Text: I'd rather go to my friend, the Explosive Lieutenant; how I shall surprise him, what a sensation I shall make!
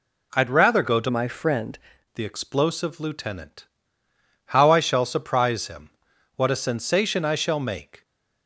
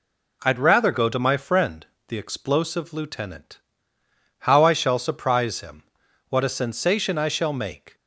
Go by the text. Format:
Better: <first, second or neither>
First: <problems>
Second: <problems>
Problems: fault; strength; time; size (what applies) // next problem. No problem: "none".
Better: second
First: changes voice from "my" to "friend"; from 1.0 to 1.7 s; 0.7 s long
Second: none